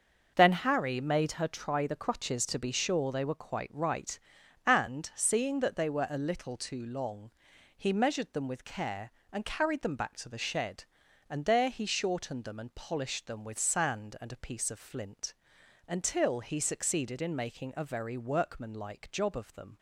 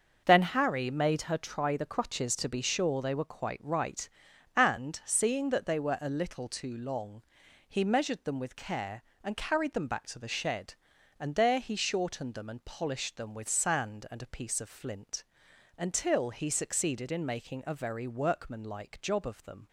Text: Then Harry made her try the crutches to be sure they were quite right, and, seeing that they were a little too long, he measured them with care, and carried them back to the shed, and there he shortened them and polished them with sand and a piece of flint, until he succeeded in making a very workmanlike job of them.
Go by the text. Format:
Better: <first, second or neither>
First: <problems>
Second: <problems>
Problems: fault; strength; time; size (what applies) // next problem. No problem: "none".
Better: neither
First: starts louder than the rest; noticeable; until 1.3 s; 6 dB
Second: starts louder than the rest; noticeable; until 1.2 s; 6 dB